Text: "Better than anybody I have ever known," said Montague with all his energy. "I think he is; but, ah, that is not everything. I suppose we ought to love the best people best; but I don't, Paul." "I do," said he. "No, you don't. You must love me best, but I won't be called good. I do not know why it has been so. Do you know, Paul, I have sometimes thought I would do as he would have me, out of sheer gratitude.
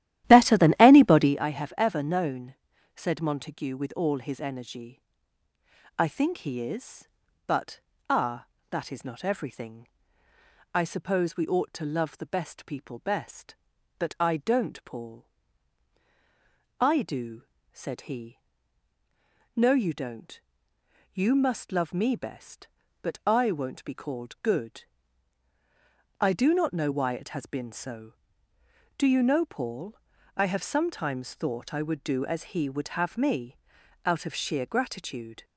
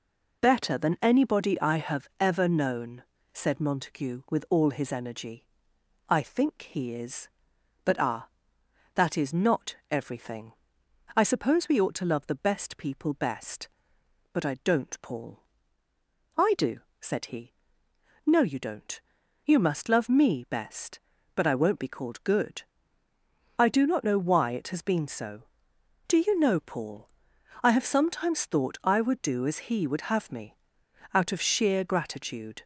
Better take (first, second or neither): second